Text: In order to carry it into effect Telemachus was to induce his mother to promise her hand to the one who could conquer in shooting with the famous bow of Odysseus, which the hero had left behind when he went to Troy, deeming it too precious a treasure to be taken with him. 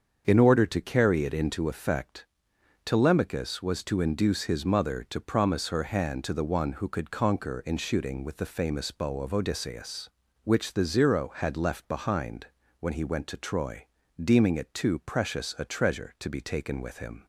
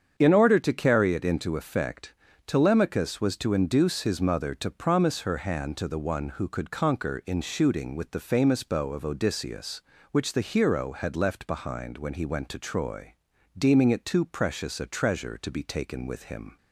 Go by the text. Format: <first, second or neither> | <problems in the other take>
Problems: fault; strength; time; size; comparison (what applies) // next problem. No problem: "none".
second | starts louder than the rest; until 1.2 s; 7 dB; strong in the second // pauses between "effect" and "Telemachus"; noticeable; at 2.2 s; 0.58 s long; slight in the second // says "zero" for "hero"; at 10.8 s // pauses between "behind" and "when"; slight; at 12.4 s; 0.32 s long